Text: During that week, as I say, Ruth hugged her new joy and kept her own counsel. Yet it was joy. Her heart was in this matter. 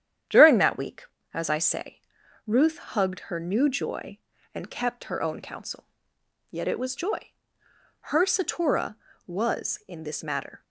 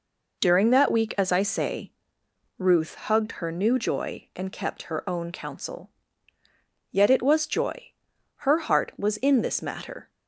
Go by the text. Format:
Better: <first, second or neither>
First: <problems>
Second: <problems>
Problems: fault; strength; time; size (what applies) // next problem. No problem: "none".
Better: second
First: starts louder than the rest; strong; until 1.5 s; 9.5 dB // says "satura" for "heart"; at 8.2 s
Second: none